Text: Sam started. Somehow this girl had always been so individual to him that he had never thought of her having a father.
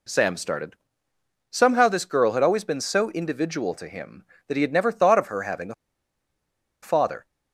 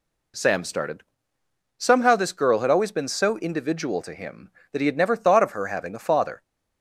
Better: second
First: pauses between "a" and "father"; at 5.7 s; 1.0 s long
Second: none

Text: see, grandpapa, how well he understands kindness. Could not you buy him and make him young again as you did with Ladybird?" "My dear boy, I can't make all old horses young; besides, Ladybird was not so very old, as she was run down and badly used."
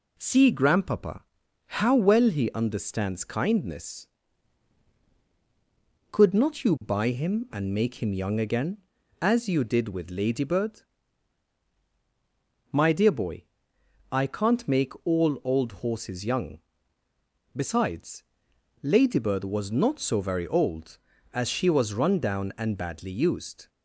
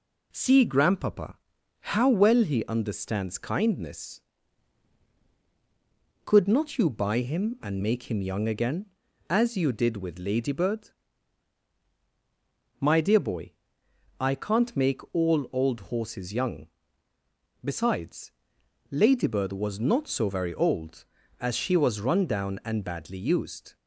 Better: neither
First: none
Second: none

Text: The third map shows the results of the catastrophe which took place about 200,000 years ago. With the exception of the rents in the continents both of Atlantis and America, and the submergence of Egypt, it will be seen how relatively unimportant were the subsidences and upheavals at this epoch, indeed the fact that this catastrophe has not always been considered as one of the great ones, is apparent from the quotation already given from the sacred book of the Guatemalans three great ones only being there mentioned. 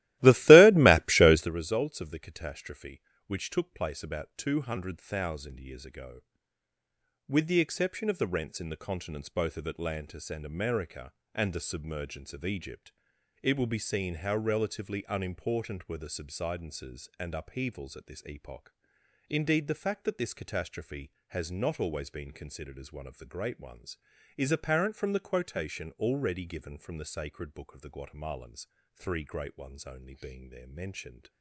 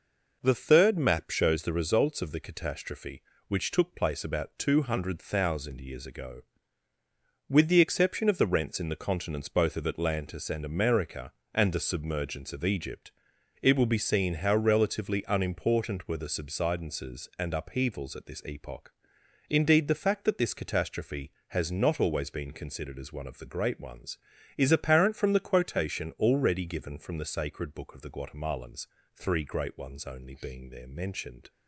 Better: second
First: starts louder than the rest; strong; until 1.5 s; 17 dB // pauses between "Guatemalans" and "three"; slight; at 28.6 s; 0.30 s long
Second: pauses between "Guatemalans" and "three"; slight; at 28.8 s; 0.30 s long

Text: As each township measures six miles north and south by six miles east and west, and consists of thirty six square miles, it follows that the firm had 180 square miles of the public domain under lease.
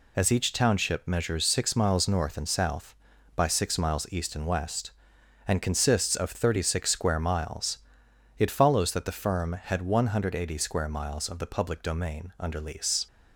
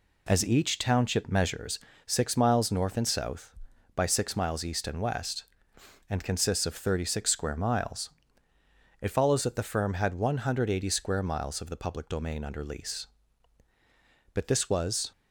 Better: first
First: none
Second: pauses between "measures" and "six"; slight; at 1.7 s; 0.26 s long // goes on to say "But this was"; noticeable; from 14.3 s on; 0.78 s long

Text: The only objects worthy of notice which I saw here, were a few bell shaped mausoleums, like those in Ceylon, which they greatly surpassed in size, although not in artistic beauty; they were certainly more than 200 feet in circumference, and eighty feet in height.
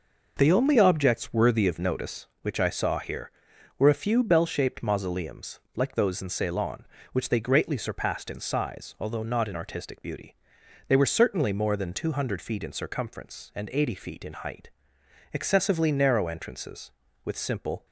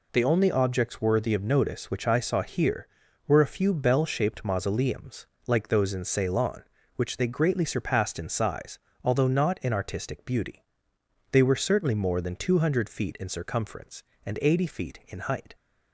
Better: second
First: goes on to say "Excessively narrow entrances with simple"; strong; from 15.3 s on; 2.5 s long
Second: none

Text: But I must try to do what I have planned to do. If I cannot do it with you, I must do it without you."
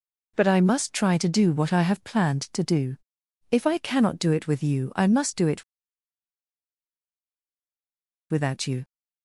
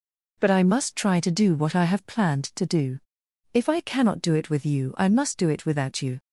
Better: second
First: pauses between "it" and "without"; strong; at 5.6 s; 2.6 s long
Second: none

